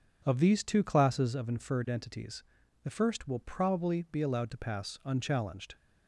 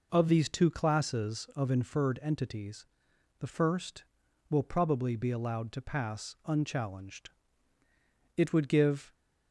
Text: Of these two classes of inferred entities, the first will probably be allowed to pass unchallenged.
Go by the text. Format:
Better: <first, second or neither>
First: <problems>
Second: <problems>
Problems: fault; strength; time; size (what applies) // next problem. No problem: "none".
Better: first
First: none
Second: goes on to say "It would give"; noticeable; from 8.3 s on; 0.78 s long